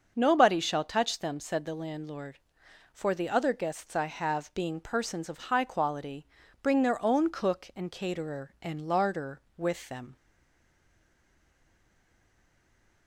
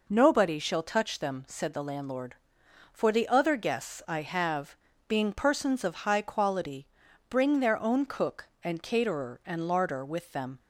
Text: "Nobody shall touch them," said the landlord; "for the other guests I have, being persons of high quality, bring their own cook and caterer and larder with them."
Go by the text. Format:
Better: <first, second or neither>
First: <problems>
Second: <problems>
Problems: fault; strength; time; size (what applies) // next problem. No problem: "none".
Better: second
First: starts louder than the rest; until 1.1 s; 6.5 dB // stays silent after the last word; strong; from 10.1 s on; 2.9 s long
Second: none